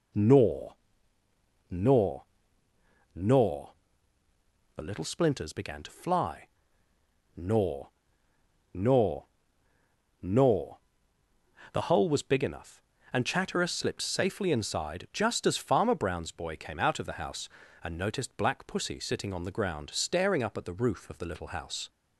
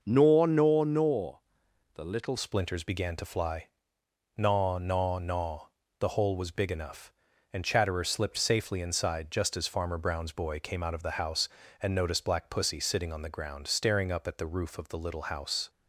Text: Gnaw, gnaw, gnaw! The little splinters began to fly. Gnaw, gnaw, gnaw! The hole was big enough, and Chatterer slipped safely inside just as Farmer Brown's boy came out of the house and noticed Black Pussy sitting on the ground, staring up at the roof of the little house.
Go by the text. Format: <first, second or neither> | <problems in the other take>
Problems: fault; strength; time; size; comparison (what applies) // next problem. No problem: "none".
first | changes voice at "splinters"; from 2.3 s on; 13.3 s long